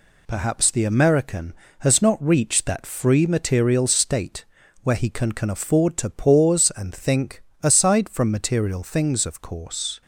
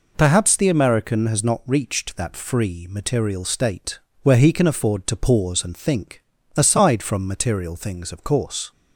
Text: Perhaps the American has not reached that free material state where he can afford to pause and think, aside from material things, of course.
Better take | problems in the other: second | pauses between "state" and "where"; at 4.4 s; 0.38 s long; slight in the second // says "can" twice; at 5.3 s

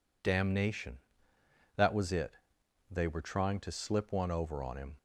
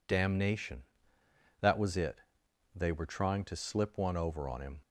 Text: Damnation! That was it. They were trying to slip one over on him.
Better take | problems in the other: neither | none

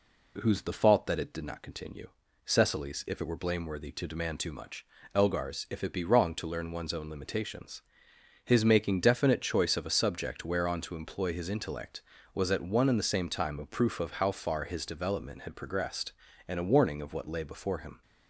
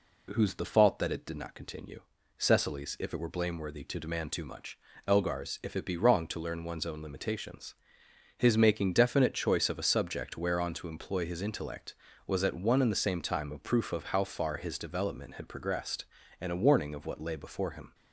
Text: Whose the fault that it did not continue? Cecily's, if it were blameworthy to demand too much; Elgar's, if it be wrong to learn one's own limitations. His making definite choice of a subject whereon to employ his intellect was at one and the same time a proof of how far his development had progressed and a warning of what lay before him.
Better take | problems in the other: neither | none

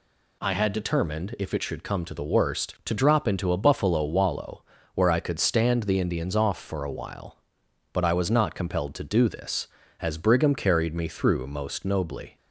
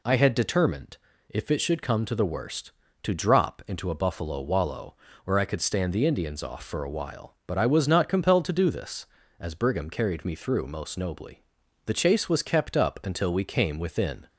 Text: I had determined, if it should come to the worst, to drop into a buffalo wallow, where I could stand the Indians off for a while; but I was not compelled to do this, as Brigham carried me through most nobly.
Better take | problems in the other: first | goes on to say "The chase was kept up until we came within"; strong; from 11.8 s on; 2.4 s long

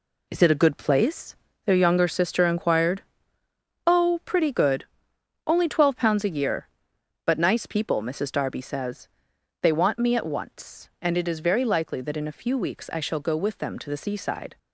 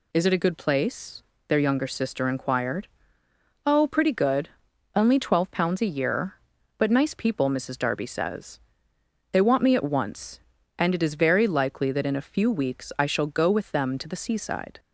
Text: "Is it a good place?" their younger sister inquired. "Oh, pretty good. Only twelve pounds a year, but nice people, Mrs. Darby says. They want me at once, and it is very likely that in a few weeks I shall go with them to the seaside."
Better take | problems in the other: second | gets quieter; strong; throughout; 8 dB

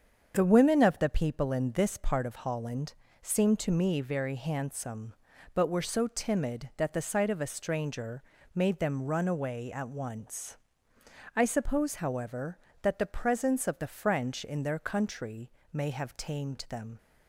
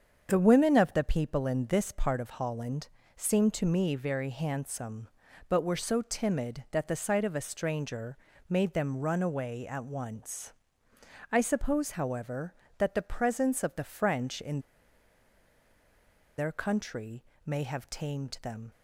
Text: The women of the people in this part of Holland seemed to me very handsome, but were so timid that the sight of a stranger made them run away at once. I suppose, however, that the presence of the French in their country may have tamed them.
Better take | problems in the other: first | starts louder than the rest; strong; until 1.3 s; 7 dB; strong in the first // pauses between "Holland" and "seemed"; slight; at 2.8 s; 0.30 s long; slight in the first // pauses between "stranger" and "made"; slight; at 8.1 s; 0.32 s long; slight in the first // pauses between "in" and "their"; strong; at 14.5 s; 1.7 s long // pauses between "country" and "may"; slight; at 17.2 s; 0.20 s long; slight in the first

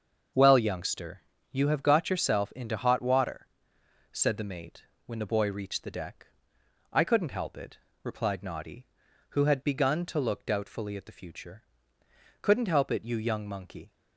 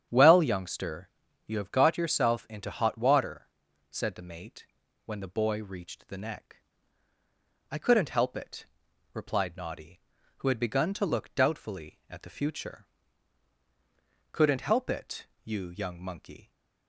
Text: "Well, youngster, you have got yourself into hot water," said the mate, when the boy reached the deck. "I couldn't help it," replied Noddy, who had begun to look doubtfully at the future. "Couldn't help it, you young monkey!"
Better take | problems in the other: first | starts louder than the rest; strong; until 1.4 s; 9 dB; also in the first // says "neck" for "deck"; at 6.1 s

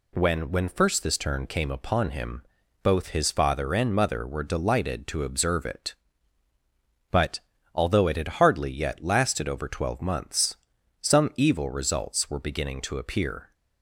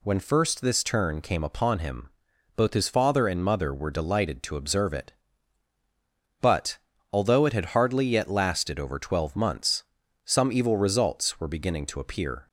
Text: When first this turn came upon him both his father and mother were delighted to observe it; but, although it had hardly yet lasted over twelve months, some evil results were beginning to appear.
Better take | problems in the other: second | says "When" twice; at 0.5 s // pauses between "him" and "both"; at 2.4 s; 0.40 s long; noticeable in the second

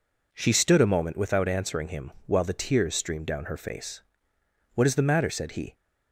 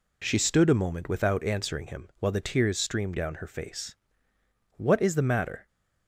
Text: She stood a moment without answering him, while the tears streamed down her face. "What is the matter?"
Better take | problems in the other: second | goes on to say "said he"; slight; from 5.2 s on; 0.46 s long

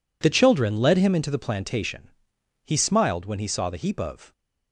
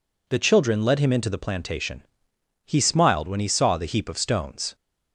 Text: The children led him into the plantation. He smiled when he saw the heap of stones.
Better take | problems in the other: second | stops before "stones"; at 4.3 s

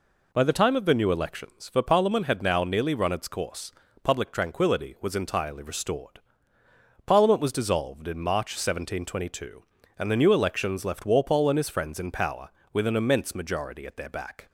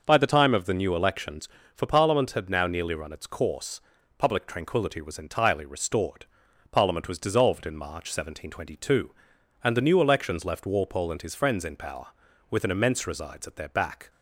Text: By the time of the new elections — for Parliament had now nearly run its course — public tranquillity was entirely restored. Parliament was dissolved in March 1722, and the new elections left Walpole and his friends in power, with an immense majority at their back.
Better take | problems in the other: first | says "resides" for "majority"; at 13.0 s

